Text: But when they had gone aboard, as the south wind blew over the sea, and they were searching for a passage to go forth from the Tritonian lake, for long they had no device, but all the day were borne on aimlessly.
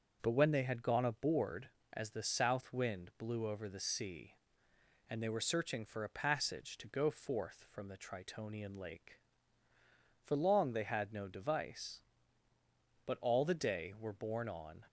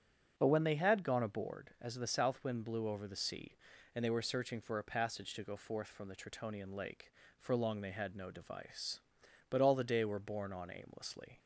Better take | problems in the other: second | starts louder than the rest; until 1.2 s; 6.5 dB; also in the second // stops before "aimlessly"; at 14.8 s

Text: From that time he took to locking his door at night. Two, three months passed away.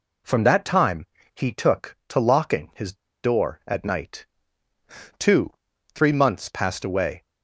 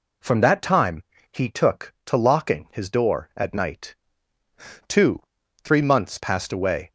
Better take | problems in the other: second | pauses between "time" and "he"; slight; at 1.0 s; 0.30 s long; slight in the second // pauses between "his" and "door"; slight; at 2.9 s; 0.28 s long

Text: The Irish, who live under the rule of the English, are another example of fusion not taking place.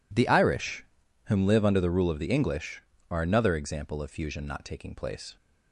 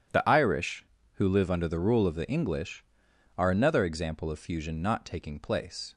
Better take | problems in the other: second | says "whom" for "who"; at 1.2 s

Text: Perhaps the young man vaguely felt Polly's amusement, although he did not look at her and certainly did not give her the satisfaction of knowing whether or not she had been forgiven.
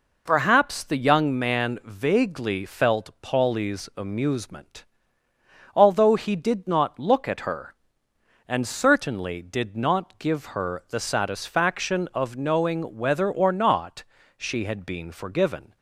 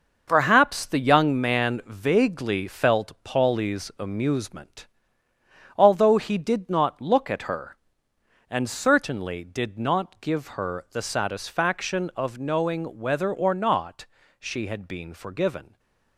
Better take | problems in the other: first | gets quieter; strong; throughout; 8.5 dB // pauses between "not" and "she"; slight; at 14.0 s; 0.34 s long; slight in the first // stays silent after the last word; slight; from 15.6 s on; 0.5 s long

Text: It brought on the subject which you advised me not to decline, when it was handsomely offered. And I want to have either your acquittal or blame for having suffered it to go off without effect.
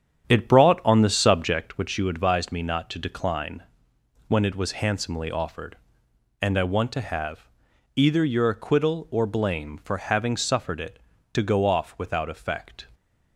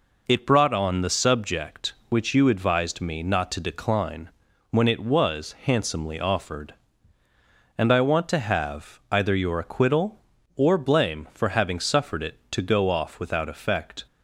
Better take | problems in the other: second | starts louder than the rest; strong; until 1.7 s; 8.5 dB // pauses between "have" and "either"; noticeable; at 7.4 s; 0.48 s long

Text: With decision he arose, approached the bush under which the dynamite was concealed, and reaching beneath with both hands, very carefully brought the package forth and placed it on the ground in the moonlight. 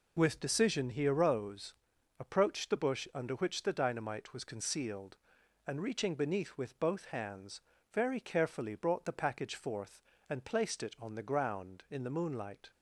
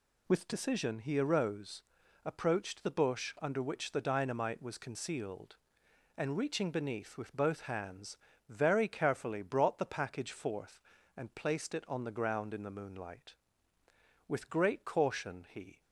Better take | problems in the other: first | goes on to say "With great caution he"; from 14.2 s on; 1.5 s long

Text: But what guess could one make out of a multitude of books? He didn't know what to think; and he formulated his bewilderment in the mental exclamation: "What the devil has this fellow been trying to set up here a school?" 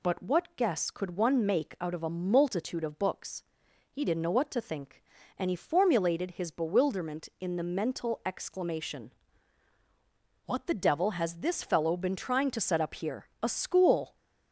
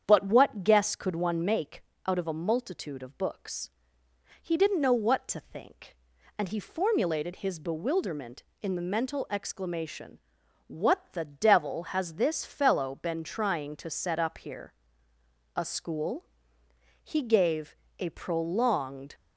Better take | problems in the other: first | starts louder than the rest; strong; until 1.0 s; 8.5 dB // pauses between "make" and "out"; slight; at 1.8 s; 0.24 s long // pauses between "here" and "a"; noticeable; at 14.7 s; 0.82 s long // goes on to say "He gave a prolonged"; strong; from 17.0 s on; 2.1 s long

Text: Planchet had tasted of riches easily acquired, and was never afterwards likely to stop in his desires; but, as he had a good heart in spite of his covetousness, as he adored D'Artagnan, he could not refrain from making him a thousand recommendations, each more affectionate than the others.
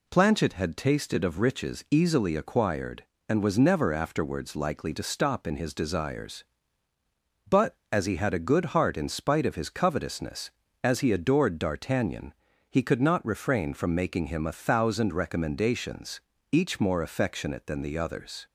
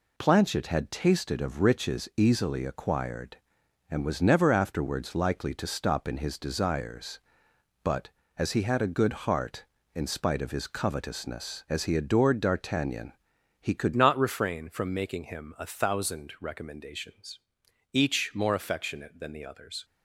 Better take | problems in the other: first | changes voice at "not"; from 13.9 s on; 5.9 s long

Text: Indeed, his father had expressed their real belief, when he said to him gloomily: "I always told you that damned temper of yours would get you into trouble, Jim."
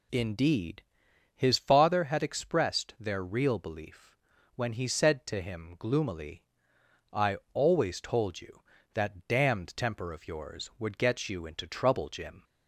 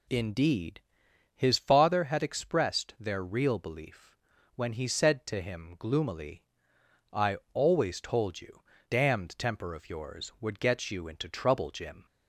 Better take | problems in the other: first | pauses between "I" and "always"; slight; at 7.3 s; 0.16 s long; slight in the first // skips "that"; at 8.7 s

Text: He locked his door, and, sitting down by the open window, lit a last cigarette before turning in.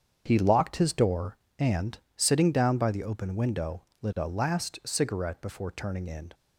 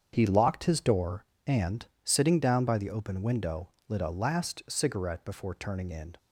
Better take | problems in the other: neither | starts louder than the rest; strong; the same in both

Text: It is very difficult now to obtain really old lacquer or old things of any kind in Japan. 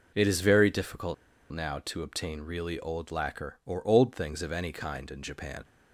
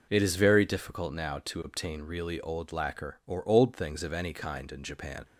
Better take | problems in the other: second | pauses between "difficult" and "now"; at 1.1 s; 0.37 s long

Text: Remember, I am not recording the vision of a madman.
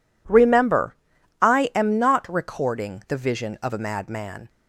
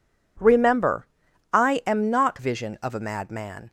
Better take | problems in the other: first | skips "recording the"; at 2.3 s

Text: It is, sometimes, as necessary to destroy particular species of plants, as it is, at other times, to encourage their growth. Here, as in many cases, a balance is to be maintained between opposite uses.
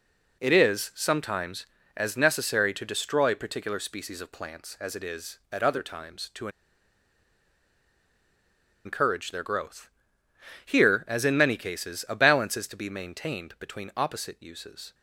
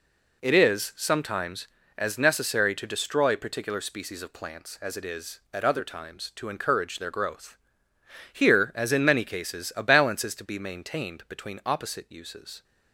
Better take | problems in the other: second | pauses between "to" and "encourage"; strong; at 6.4 s; 2.3 s long

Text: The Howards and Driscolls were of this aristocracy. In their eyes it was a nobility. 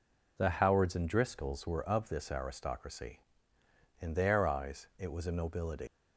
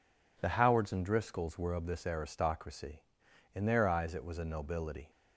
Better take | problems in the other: second | leaves "nobility" unfinished; at 5.8 s; 165 ms

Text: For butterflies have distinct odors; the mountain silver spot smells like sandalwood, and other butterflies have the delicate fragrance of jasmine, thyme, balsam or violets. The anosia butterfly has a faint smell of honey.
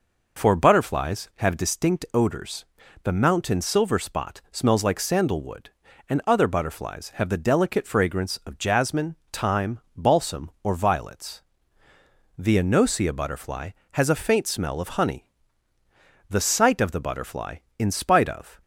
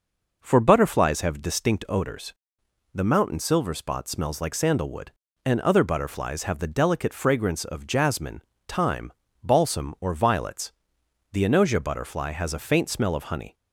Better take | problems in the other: second | goes on to say "The sight of the butterfly in spite of"; strong; from 16.2 s on; 2.3 s long

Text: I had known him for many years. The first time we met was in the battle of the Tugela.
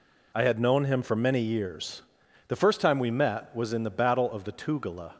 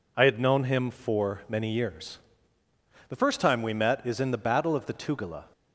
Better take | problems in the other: first | says "is" for "was"; at 4.0 s

